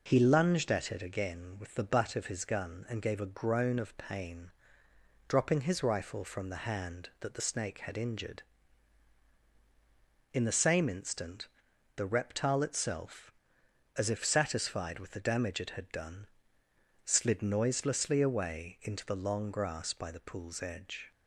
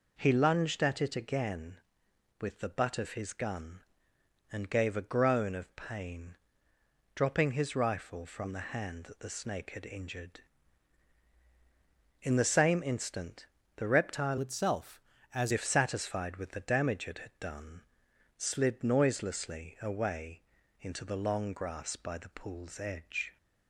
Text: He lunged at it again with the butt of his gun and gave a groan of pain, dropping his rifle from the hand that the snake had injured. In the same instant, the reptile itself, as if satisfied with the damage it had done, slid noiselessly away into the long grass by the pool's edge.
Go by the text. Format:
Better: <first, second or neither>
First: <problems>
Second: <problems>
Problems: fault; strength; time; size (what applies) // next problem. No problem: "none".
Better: first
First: none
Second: changes voice from "itself" to "as"; from 14.4 to 15.5 s; 1.1 s long // pauses between "away" and "into"; at 20.4 s; 0.40 s long